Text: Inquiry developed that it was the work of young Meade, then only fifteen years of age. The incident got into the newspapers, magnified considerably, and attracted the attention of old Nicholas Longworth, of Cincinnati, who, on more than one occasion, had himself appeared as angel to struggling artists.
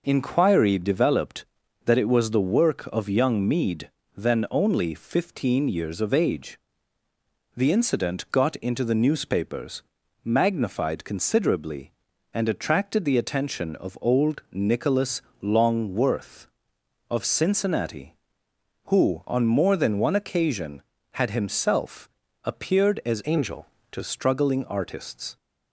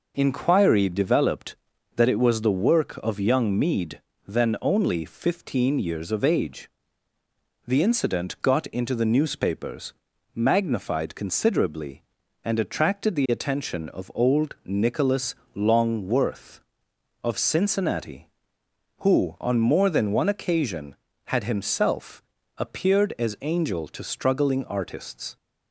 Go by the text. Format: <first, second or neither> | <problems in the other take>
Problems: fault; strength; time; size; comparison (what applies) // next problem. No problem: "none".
second | pauses between "Nicholas" and "Longworth"; slight; at 15.2 s; 0.18 s long; slight in the second // pauses between "himself" and "appeared"; slight; at 22.1 s; 0.32 s long; slight in the second // changes voice from "angel" to "to"; from 23.2 to 24.0 s; 0.8 s long